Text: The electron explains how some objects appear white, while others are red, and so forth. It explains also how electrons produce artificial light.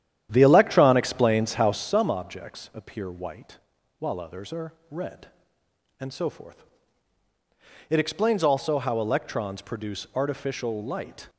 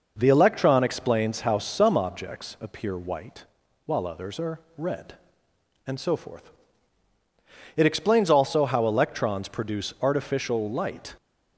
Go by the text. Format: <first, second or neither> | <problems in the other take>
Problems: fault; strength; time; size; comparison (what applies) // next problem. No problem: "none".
second | starts louder than the rest; strong; until 1.9 s; 10.5 dB // pauses between "are" and "red"; slight; at 4.7 s; 0.16 s long; slight in the second